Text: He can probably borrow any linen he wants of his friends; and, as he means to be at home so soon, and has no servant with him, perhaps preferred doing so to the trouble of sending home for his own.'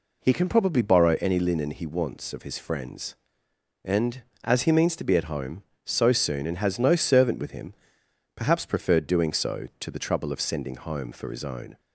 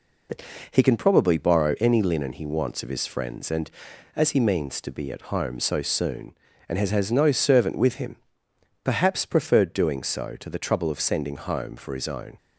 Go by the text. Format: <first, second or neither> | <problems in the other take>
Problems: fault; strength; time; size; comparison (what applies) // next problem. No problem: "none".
first | says "has" twice; at 6.9 s